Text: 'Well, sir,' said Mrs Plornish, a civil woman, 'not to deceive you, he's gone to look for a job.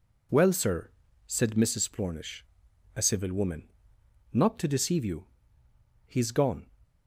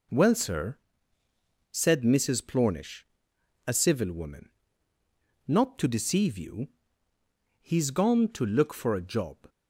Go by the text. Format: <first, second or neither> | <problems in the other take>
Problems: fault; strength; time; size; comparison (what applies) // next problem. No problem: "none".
second | stops before "to look for a job"; at 6.8 s